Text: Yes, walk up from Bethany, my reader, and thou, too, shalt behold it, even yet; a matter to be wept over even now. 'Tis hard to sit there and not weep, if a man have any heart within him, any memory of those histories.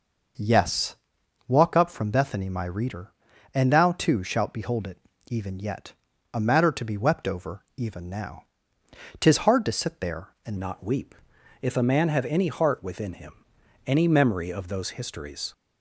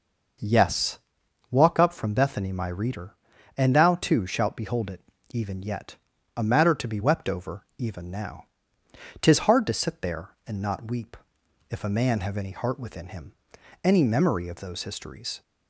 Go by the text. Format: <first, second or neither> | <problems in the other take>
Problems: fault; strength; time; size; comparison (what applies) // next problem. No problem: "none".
second | changes voice at "not"; from 10.5 s on; 5.0 s long